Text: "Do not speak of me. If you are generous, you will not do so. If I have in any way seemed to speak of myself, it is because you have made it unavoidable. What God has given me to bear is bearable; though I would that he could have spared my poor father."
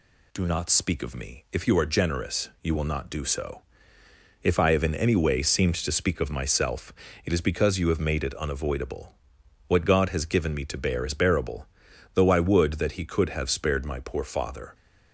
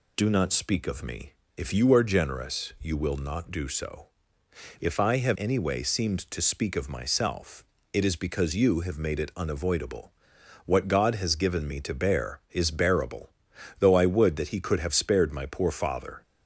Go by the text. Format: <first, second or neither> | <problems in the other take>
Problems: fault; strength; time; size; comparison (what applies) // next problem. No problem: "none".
first | skips "in"; at 5.3 s